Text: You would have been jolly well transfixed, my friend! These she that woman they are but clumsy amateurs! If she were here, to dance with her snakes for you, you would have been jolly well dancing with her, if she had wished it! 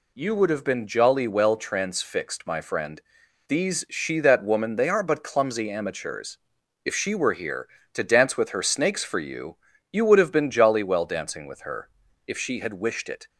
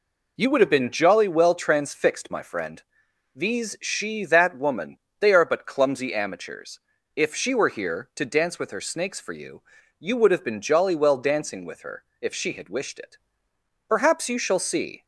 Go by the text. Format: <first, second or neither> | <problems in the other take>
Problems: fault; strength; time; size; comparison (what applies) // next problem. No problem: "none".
first | pauses between "woman" and "they"; slight; at 4.9 s; 0.22 s long // goes on to say "Perhaps you shall see"; noticeable; from 13.8 s on; 1.1 s long